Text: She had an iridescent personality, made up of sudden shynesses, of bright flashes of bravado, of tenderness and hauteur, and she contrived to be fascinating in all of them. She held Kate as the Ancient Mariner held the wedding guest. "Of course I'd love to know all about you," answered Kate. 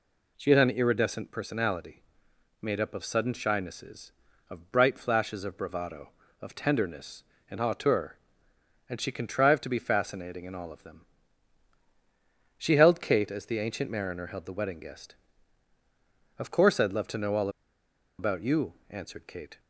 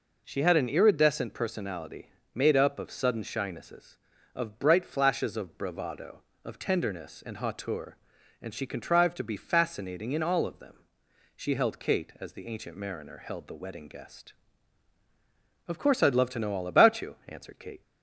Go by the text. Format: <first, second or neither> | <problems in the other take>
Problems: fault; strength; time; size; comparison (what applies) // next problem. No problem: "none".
second | pauses between "all" and "about"; noticeable; at 17.4 s; 0.70 s long